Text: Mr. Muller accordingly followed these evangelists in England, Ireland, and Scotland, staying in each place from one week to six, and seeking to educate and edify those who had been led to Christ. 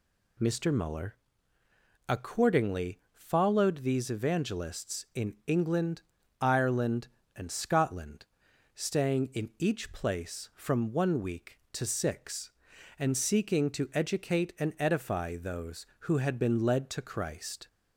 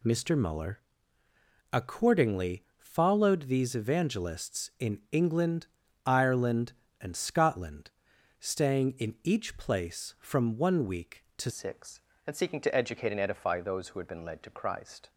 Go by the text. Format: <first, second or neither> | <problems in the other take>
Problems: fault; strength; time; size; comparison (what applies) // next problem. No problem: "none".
first | pauses between "Muller" and "accordingly"; noticeable; at 0.8 s; 0.92 s long; noticeable in the first // changes voice at "six"; from 11.5 s on; 3.5 s long